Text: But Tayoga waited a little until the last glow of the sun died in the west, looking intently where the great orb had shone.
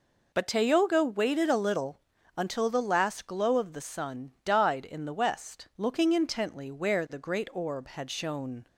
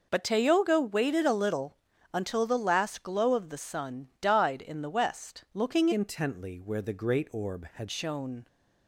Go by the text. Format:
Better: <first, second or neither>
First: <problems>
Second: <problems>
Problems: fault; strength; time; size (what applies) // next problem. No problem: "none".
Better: first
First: pauses between "little" and "until"; at 2.0 s; 0.38 s long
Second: pauses between "little" and "until"; at 1.7 s; 0.38 s long // changes voice from "intently" to "had"; from 5.9 to 7.8 s; 1.9 s long